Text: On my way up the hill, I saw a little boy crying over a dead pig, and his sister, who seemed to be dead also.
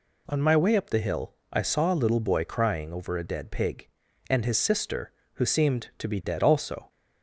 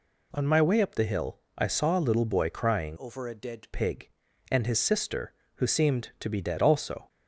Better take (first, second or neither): first